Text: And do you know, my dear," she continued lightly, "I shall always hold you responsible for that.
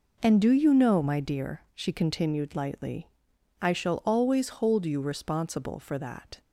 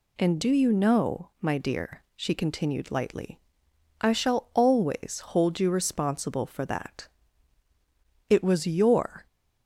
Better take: first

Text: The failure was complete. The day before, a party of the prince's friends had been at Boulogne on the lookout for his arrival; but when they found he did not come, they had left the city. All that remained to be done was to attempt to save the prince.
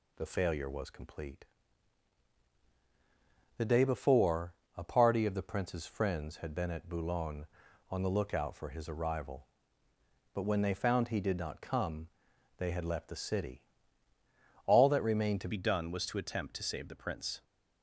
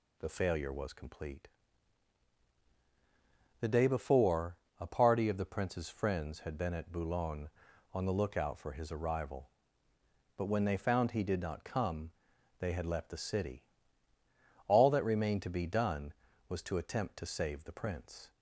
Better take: second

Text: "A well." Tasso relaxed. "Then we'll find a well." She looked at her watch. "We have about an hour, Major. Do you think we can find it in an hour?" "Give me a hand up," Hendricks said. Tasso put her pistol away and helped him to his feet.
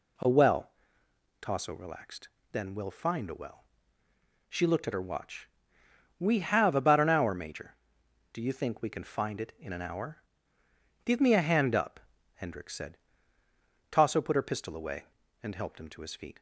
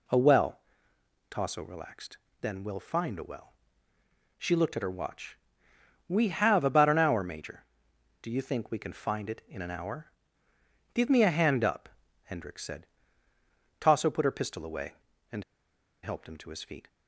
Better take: first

